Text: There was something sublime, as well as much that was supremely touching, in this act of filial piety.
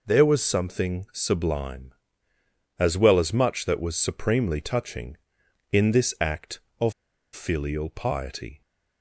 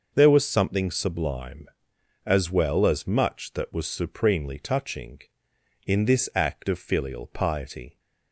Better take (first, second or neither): second